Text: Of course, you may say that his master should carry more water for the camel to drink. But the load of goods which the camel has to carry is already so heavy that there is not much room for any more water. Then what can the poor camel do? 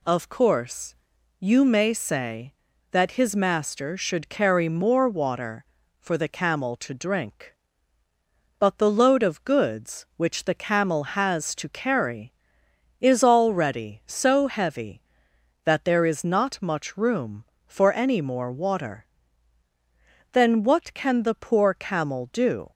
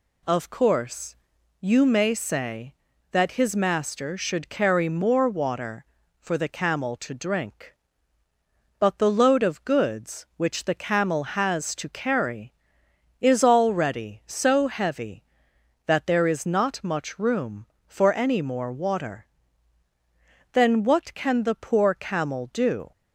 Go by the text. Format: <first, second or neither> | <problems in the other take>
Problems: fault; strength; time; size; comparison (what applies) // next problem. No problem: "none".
neither | none